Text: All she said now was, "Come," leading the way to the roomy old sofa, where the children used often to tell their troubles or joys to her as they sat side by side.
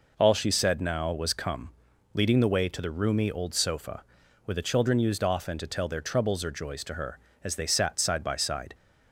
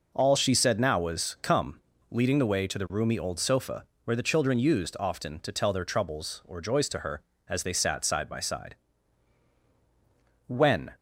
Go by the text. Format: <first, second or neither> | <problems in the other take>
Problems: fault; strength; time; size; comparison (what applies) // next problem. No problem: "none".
first | goes on to say "When"; slight; from 10.4 s on; 0.46 s long